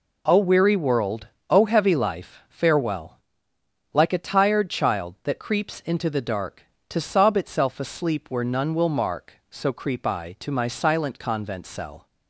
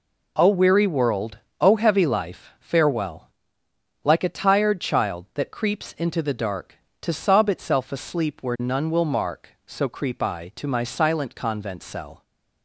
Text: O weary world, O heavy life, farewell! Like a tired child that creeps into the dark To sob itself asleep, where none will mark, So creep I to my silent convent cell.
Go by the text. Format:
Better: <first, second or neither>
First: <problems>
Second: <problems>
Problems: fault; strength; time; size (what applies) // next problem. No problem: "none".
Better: neither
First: none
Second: none